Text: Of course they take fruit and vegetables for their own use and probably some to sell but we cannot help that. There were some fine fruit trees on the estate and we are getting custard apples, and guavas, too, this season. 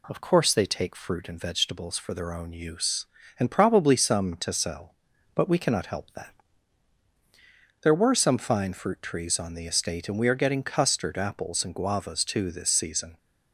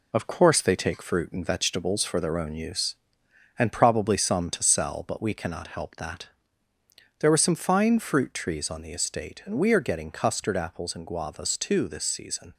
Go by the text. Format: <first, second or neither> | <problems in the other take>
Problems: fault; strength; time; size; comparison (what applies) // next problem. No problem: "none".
first | gets quieter; noticeable; throughout; 4.5 dB